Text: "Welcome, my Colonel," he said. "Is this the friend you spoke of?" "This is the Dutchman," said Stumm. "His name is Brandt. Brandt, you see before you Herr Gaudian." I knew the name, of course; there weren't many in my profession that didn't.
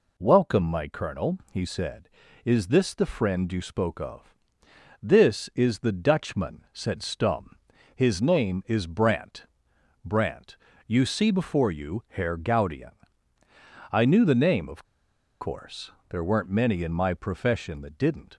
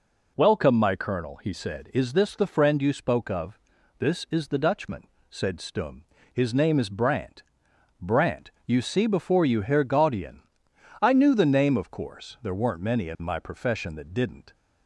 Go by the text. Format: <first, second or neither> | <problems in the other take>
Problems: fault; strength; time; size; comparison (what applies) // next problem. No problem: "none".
second | pauses between "of" and "course"; noticeable; at 14.8 s; 0.57 s long